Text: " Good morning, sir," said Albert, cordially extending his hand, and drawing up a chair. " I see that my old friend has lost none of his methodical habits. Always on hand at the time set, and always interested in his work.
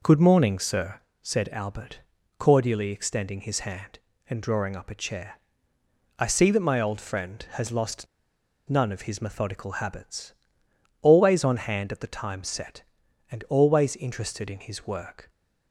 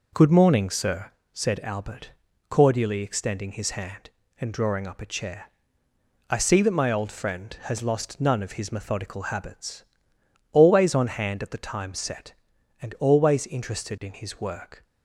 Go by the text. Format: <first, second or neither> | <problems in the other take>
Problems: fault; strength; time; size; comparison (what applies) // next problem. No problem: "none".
second | pauses between "lost" and "none"; noticeable; at 8.0 s; 0.62 s long